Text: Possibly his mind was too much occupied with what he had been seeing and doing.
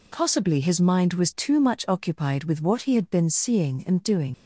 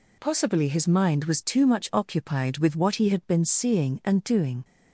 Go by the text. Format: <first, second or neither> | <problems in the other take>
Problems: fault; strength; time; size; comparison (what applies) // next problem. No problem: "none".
second | leaves "doing" unfinished; at 4.3 s; 90 ms